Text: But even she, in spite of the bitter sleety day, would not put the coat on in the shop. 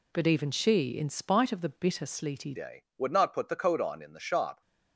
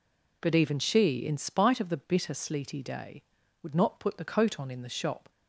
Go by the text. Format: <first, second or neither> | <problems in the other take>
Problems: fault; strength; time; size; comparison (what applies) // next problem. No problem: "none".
second | changes voice at "day"; from 2.5 s on; 2.1 s long